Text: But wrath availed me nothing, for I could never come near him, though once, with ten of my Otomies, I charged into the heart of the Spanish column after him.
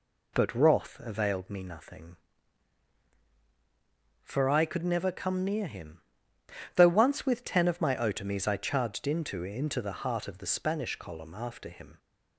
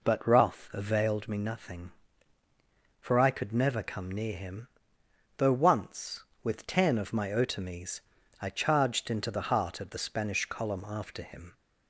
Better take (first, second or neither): second